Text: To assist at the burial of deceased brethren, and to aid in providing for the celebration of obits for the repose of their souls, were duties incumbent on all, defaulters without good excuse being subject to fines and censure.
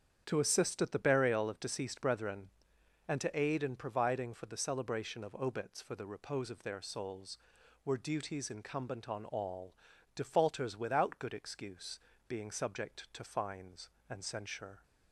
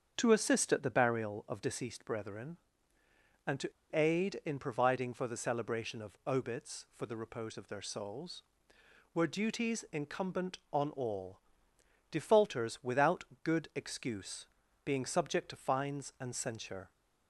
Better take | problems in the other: first | starts louder than the rest; strong; until 1.1 s; 7.5 dB; strong in the first // pauses between "to" and "aid"; slight; at 3.7 s; 0.21 s long // pauses between "without" and "good"; slight; at 13.2 s; 0.20 s long // pauses between "excuse" and "being"; at 14.4 s; 0.40 s long; slight in the first

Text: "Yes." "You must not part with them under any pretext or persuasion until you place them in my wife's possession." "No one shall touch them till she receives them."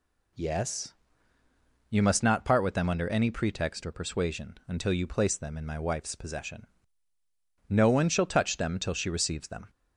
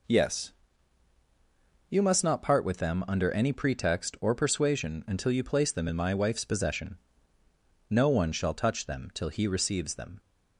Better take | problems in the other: first | says "he" for "she"; at 9.2 s

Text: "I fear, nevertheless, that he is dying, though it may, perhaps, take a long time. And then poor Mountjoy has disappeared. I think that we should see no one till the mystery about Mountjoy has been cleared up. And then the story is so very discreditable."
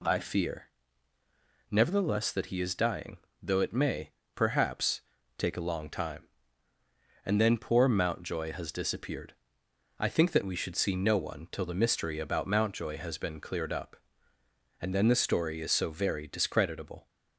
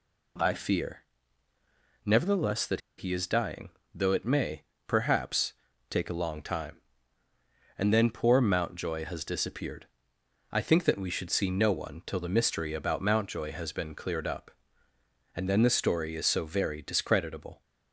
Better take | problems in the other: first | pauses between "that" and "he"; slight; at 2.8 s; 0.17 s long

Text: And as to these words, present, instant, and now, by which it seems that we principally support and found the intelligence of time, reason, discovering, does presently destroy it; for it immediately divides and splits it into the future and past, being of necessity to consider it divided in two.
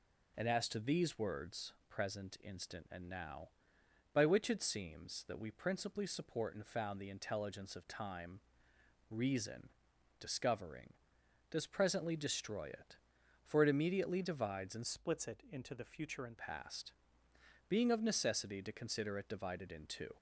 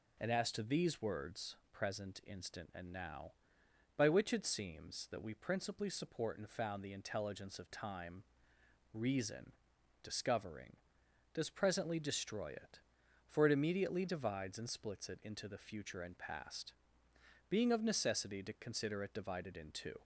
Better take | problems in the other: second | changes voice from "splits" to "and"; from 14.8 to 16.3 s; 1.5 s long

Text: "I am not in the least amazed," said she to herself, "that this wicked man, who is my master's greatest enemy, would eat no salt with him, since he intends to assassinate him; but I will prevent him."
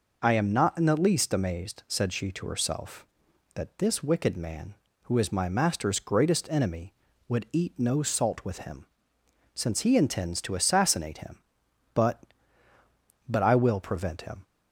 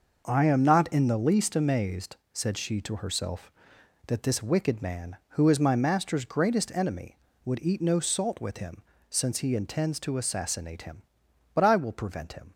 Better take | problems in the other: second | says "but" twice; at 13.2 s

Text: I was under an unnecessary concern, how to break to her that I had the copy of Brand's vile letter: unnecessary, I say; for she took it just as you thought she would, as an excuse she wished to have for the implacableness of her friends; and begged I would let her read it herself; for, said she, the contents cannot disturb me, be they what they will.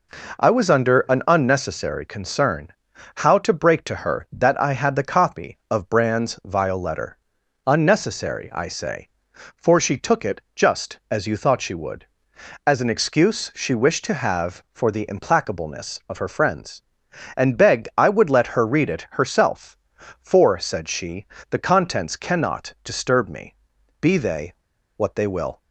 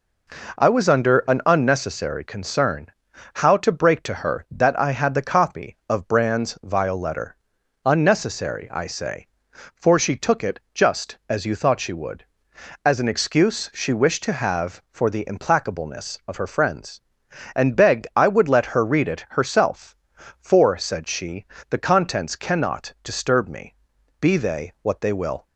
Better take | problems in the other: second | pauses between "they" and "what"; at 24.5 s; 0.43 s long

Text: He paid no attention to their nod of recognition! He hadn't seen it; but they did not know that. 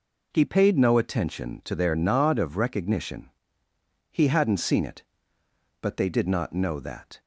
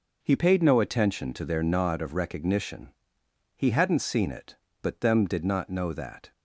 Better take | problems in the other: first | says "them" for "they"; at 5.0 s

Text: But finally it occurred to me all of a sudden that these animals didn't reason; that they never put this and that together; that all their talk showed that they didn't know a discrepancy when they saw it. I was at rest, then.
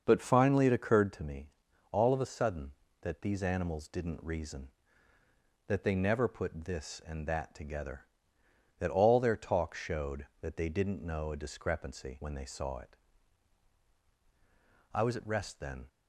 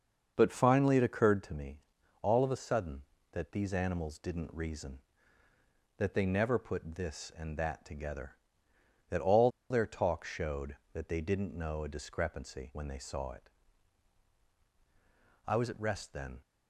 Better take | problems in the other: first | starts louder than the rest; until 1.3 s; 6.5 dB; also in the first // pauses between "me" and "all"; at 1.7 s; 0.44 s long; also in the first // pauses between "all" and "their"; slight; at 9.4 s; 0.21 s long

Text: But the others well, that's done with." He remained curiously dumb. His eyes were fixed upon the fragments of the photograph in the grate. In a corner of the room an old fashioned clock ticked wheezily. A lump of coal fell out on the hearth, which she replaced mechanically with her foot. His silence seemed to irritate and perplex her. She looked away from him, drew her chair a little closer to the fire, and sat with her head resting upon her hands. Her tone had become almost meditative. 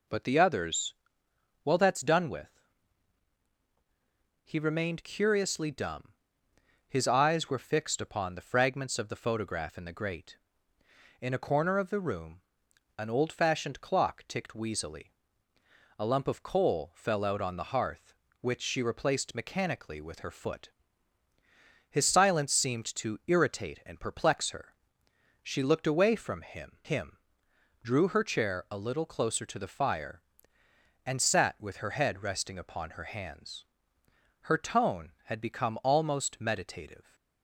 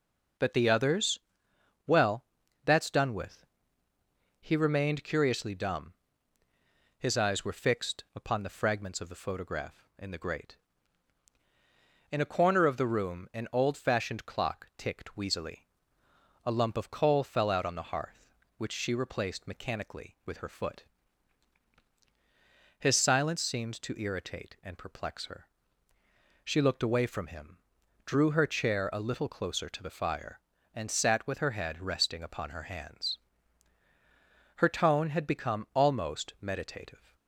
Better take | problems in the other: second | pauses between "others" and "well"; noticeable; at 0.9 s; 0.72 s long; noticeable in the second // pauses between "room" and "an"; noticeable; at 12.4 s; 0.56 s long // says "him" twice; at 26.8 s

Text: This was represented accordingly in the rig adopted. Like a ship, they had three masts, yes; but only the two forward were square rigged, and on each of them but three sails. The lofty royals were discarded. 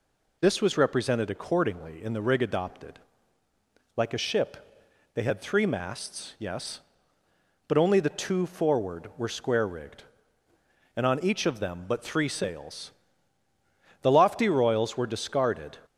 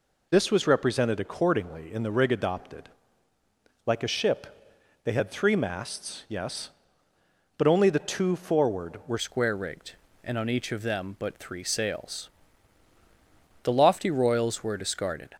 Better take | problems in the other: first | changes voice at "square"; from 9.1 s on; 6.2 s long

